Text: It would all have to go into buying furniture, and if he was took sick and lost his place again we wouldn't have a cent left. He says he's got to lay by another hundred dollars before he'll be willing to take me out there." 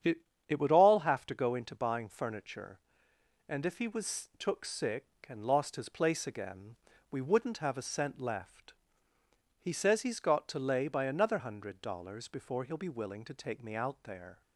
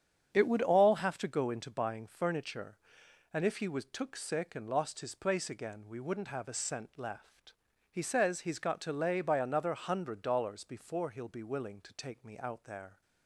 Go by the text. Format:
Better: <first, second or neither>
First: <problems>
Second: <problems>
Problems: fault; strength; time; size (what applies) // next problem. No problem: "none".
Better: second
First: starts louder than the rest; strong; until 1.3 s; 8.5 dB // says "It" twice; at 0.4 s // pauses between "again" and "we"; at 6.7 s; 0.38 s long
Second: starts louder than the rest; strong; until 1.3 s; 8 dB